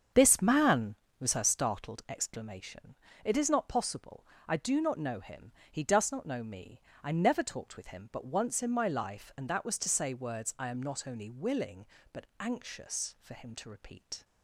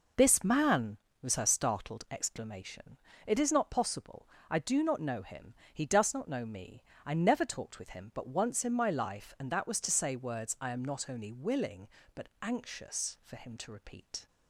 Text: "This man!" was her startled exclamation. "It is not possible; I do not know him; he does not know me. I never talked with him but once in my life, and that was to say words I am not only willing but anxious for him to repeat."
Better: second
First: starts louder than the rest; strong; until 1.4 s; 7.5 dB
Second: none

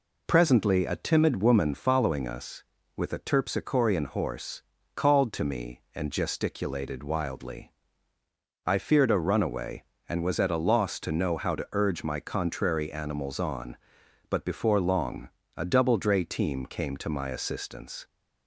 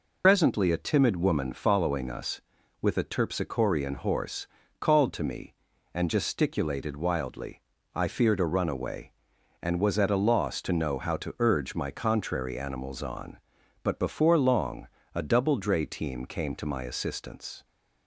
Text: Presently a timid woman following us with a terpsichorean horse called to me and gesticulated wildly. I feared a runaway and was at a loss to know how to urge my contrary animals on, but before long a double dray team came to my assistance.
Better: first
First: pauses between "horse" and "called"; slight; at 4.6 s; 0.34 s long // pauses between "long" and "a"; slight; at 15.2 s; 0.26 s long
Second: loses the start of "Presently"; at 0.2 s; 85 ms // pauses between "horse" and "called"; slight; at 4.4 s; 0.32 s long // pauses between "long" and "a"; slight; at 14.8 s; 0.28 s long

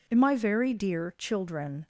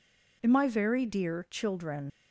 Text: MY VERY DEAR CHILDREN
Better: first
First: none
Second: leaves "CHILDREN" unfinished; at 2.1 s; 90 ms

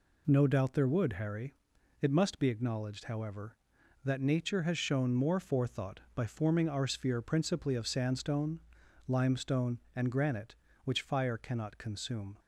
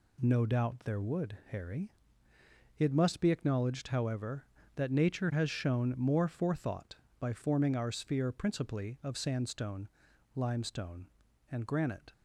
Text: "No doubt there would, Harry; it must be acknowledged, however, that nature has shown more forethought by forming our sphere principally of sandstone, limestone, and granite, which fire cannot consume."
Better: first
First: none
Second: stops before "which fire cannot consume"; at 12.1 s

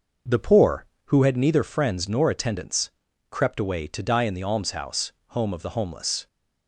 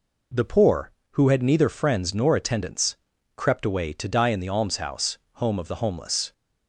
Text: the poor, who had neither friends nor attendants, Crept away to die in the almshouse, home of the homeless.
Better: second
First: starts louder than the rest; noticeable; until 1.4 s; 6 dB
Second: none

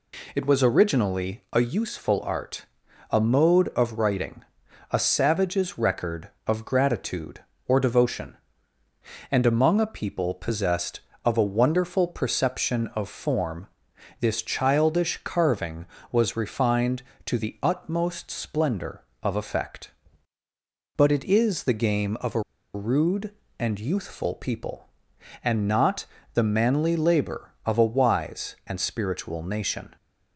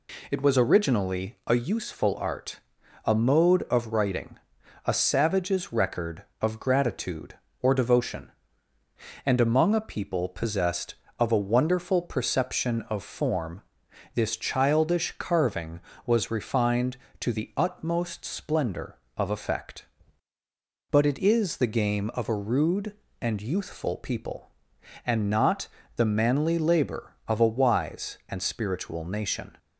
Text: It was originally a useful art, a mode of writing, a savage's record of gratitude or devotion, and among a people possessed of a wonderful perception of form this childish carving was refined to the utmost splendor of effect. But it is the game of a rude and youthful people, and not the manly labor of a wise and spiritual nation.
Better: second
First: pauses between "form" and "this"; noticeable; at 13.6 s; 0.52 s long // pauses between "a" and "rude"; slight; at 22.4 s; 0.34 s long // pauses between "not" and "the"; slight; at 26.0 s; 0.30 s long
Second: pauses between "form" and "this"; noticeable; at 13.6 s; 0.52 s long // pauses between "not" and "the"; slight; at 25.6 s; 0.30 s long

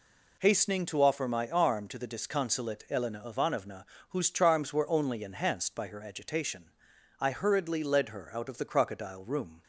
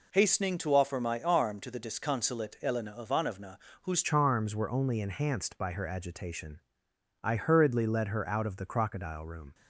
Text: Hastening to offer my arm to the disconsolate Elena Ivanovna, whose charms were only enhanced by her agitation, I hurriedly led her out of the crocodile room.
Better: first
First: none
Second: changes voice at "charms"; from 4.0 s on; 5.5 s long

